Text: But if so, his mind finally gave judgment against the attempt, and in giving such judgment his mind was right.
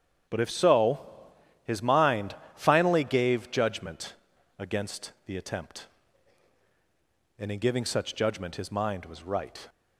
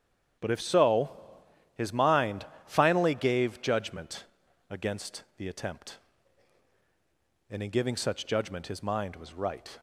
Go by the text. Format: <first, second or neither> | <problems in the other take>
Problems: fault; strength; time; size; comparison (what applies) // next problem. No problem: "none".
neither | starts louder than the rest; strong; the same in both // pauses between "mind" and "finally"; slight; the same in both // pauses between "judgment" and "against"; the same in both